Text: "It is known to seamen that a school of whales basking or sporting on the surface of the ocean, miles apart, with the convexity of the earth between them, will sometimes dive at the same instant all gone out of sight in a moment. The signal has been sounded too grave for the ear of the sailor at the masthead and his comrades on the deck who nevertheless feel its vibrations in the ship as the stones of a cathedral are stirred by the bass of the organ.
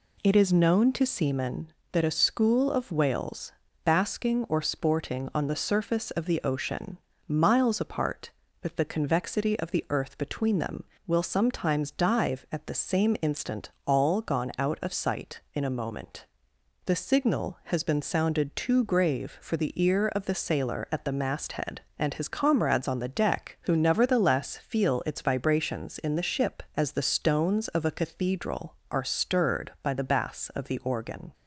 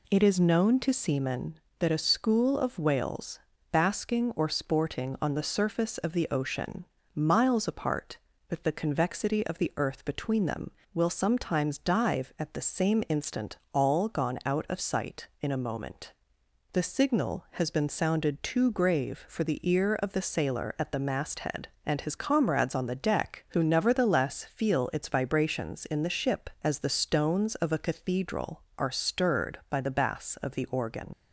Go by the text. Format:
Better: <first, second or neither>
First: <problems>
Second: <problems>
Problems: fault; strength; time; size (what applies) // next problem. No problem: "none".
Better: first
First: pauses between "whales" and "basking"; slight; at 3.5 s; 0.32 s long // pauses between "instant" and "all"; slight; at 13.7 s; 0.16 s long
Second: pauses between "whales" and "basking"; slight; at 3.3 s; 0.32 s long // pauses between "instant" and "all"; slight; at 13.5 s; 0.16 s long // leaves "organ" unfinished; at 31.1 s; 65 ms